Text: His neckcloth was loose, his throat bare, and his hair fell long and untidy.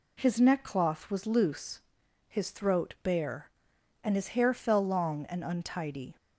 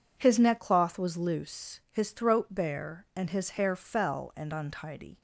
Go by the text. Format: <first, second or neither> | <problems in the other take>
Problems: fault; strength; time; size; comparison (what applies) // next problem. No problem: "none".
first | skips "long"; at 4.3 s